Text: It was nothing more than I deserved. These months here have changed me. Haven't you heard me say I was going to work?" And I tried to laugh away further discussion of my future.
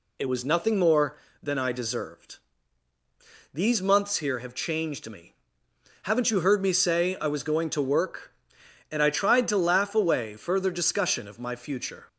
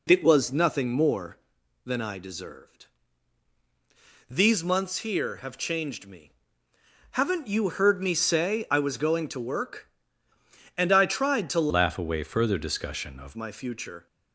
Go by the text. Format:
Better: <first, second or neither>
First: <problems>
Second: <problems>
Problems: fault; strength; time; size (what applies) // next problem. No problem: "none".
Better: first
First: none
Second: changes voice from "laugh" to "of"; from 11.6 to 13.3 s; 1.7 s long